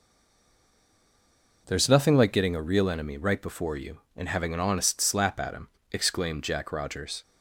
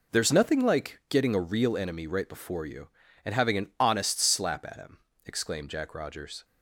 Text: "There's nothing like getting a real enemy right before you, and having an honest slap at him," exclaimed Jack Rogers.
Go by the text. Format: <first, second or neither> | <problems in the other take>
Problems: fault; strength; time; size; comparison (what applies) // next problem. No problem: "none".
second | stays silent before the first word; noticeable; until 1.6 s; 1.6 s long